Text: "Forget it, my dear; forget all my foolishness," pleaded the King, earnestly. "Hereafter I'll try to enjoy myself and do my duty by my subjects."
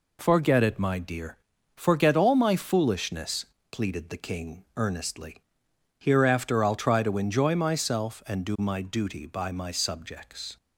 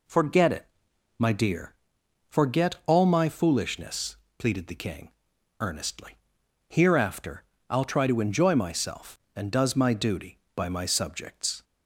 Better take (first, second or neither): first